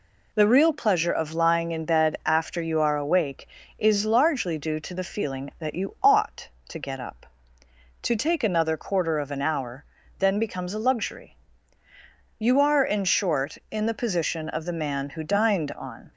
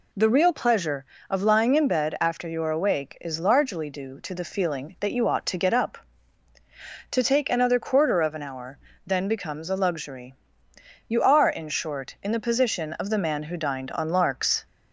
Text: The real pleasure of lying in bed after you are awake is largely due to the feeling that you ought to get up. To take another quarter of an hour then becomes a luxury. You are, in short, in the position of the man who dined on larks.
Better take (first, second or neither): second